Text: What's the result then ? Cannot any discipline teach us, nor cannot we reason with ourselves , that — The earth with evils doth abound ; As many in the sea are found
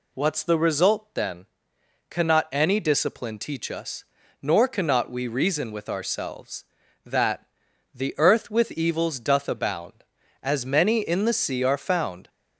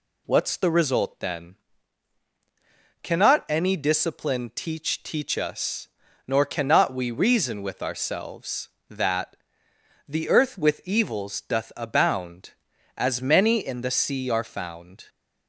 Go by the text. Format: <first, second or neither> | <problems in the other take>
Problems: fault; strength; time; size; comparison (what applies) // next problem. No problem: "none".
first | says "teach" twice; at 5.0 s